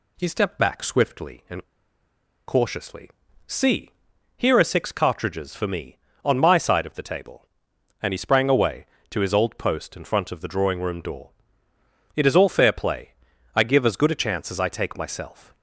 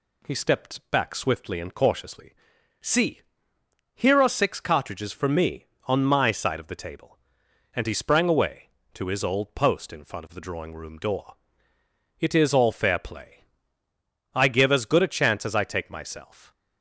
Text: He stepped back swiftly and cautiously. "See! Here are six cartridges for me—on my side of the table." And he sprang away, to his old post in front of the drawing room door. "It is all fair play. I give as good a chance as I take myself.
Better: second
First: pauses between "and" and "cautiously"; noticeable; at 1.6 s; 0.85 s long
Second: none

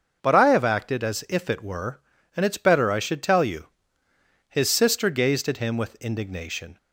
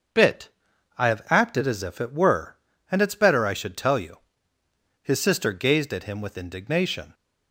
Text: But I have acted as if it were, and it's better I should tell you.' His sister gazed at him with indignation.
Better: first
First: starts louder than the rest; until 1.2 s; 6.5 dB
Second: starts louder than the rest; until 1.7 s; 6.5 dB // says "Bit" for "But"; at 0.1 s

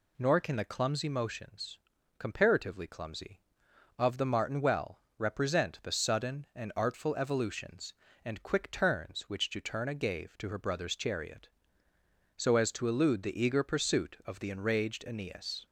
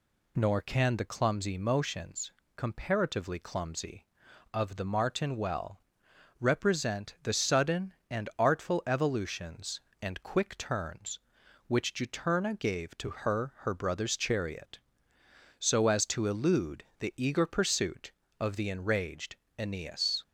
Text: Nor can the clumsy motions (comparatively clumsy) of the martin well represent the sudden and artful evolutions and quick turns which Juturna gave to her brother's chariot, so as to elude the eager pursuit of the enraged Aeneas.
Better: first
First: pauses between "well" and "represent"; slight; at 5.0 s; 0.16 s long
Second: pauses between "well" and "represent"; noticeable; at 5.8 s; 0.60 s long // says "her" twice; at 13.6 s // pauses between "enraged" and "Aeneas"; slight; at 19.3 s; 0.20 s long

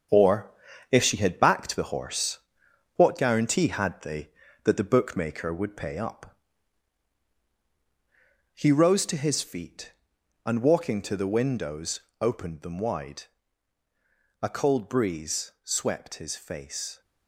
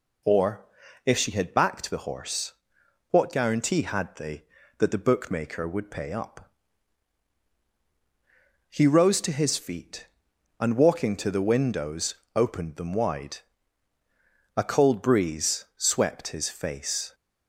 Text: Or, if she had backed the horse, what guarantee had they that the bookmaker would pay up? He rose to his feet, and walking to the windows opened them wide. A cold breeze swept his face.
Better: second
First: gets quieter; throughout; 6.5 dB // pauses between "windows" and "opened"; slight; at 12.0 s; 0.20 s long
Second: pauses between "windows" and "opened"; slight; at 12.1 s; 0.20 s long

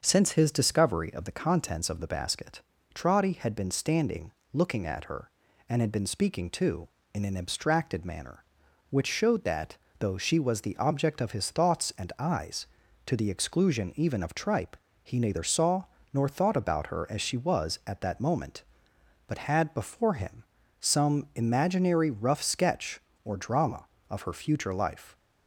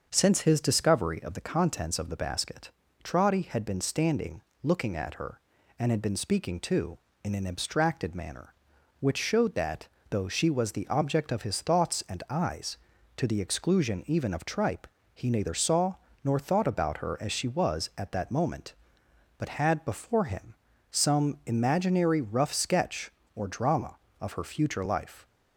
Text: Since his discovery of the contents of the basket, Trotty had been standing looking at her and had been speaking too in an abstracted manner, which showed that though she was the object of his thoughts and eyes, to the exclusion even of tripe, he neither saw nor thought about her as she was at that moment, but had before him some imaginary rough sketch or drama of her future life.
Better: neither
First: starts louder than the rest; until 1.0 s; 6.5 dB // pauses between "standing" and "looking"; slight; at 4.3 s; 0.22 s long // pauses between "that" and "though"; slight; at 9.7 s; 0.24 s long // pauses between "saw" and "nor"; slight; at 15.8 s; 0.30 s long // pauses between "him" and "some"; slight; at 20.4 s; 0.36 s long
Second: starts louder than the rest; until 1.1 s; 6.5 dB // pauses between "standing" and "looking"; slight; at 4.4 s; 0.22 s long // pauses between "that" and "though"; slight; at 9.8 s; 0.24 s long // pauses between "saw" and "nor"; slight; at 15.9 s; 0.30 s long // pauses between "him" and "some"; slight; at 20.5 s; 0.36 s long

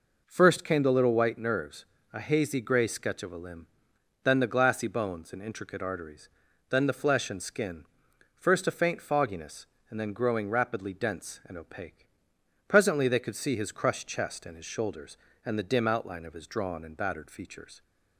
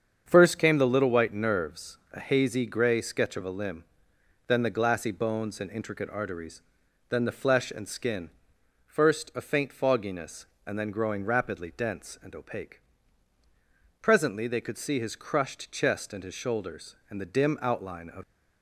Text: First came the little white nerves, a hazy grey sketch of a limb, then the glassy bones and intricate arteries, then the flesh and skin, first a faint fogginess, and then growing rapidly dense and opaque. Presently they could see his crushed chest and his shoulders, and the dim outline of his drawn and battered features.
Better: first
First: none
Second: starts louder than the rest; strong; until 1.2 s; 7 dB // stops before "his drawn and battered features"; at 18.2 s

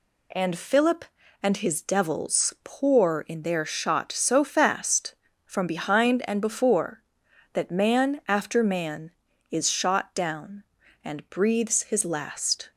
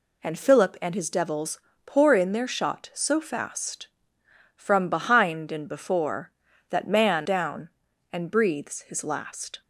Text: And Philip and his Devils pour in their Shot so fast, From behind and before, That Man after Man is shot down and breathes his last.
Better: first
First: none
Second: pauses between "Devils" and "pour"; slight; at 1.5 s; 0.26 s long // skips "after Man is shot"; at 7.2 s

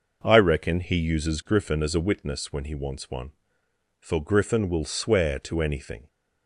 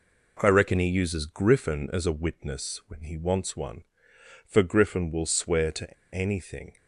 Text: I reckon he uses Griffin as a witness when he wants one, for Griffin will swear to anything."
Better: first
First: none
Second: pauses between "to" and "anything"; slight; at 5.9 s; 0.20 s long

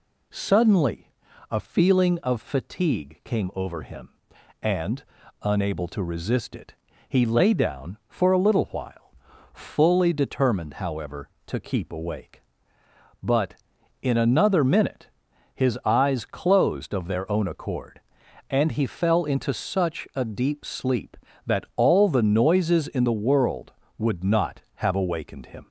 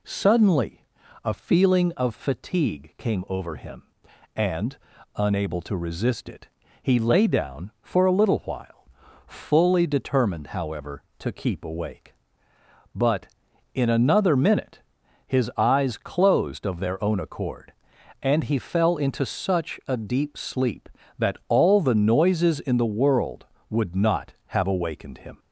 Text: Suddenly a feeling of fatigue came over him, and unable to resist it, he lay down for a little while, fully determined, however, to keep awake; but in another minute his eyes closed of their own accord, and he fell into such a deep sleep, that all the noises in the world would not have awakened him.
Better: neither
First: pauses between "Suddenly" and "a"; at 1.1 s; 0.38 s long // pauses between "and" and "unable"; at 5.0 s; 0.38 s long // pauses between "minute" and "his"; noticeable; at 15.0 s; 0.48 s long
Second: pauses between "Suddenly" and "a"; at 0.8 s; 0.38 s long // pauses between "and" and "unable"; at 4.7 s; 0.38 s long // pauses between "minute" and "his"; noticeable; at 14.7 s; 0.48 s long

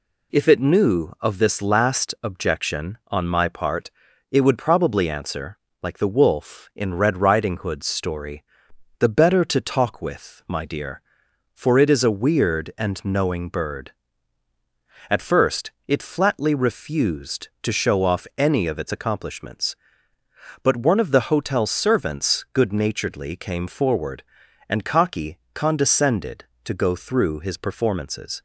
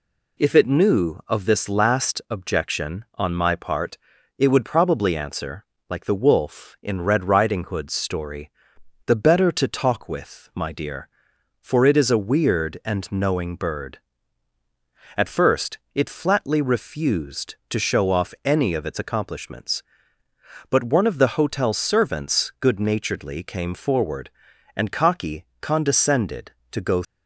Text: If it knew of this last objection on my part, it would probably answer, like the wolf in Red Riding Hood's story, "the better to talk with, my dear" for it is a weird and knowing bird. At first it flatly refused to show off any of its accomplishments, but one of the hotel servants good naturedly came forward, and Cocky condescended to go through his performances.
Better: first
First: none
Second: stops before "through his performances"; at 27.0 s

